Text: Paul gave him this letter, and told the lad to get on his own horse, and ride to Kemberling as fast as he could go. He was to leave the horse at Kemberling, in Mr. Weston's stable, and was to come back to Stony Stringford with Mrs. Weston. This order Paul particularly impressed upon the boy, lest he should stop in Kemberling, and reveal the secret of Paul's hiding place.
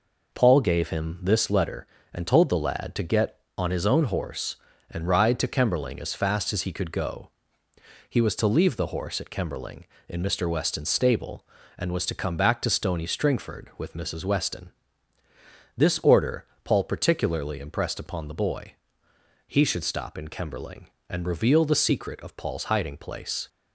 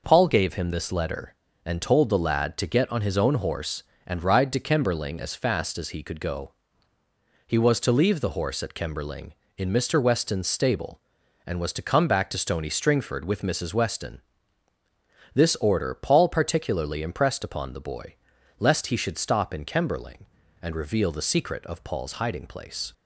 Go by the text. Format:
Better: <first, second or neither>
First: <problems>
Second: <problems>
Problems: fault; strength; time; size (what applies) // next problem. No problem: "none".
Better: second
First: pauses between "order" and "Paul"; slight; at 16.4 s; 0.20 s long // skips "lest"; at 19.1 s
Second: none